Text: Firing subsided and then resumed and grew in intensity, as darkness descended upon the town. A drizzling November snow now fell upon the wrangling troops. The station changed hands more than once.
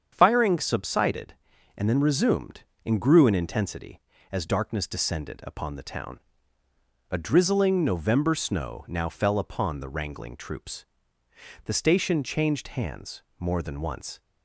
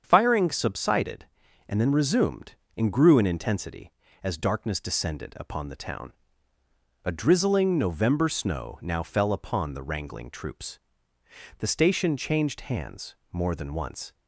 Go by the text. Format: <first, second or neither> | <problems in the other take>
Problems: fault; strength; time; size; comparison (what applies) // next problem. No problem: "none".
neither | starts louder than the rest; strong; the same in both // pauses between "hands" and "more"; slight; the same in both